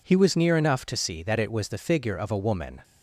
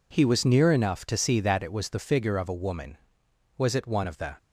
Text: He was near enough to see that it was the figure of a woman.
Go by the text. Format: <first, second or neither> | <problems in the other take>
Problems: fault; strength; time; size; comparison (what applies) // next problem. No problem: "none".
first | goes on to say "Was it one of the"; noticeable; from 3.5 s on; 0.78 s long